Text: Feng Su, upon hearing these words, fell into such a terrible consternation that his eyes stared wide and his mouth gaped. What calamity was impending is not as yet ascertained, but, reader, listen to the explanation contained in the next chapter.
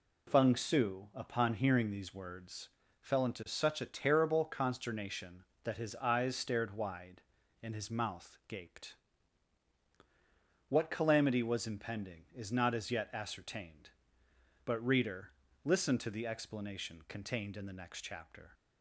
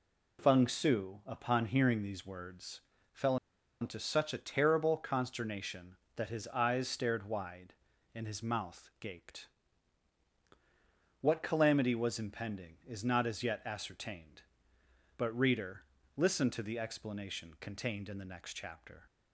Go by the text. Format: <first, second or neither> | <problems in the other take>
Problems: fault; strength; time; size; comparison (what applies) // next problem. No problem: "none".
first | pauses between "fell" and "into"; at 3.3 s; 0.45 s long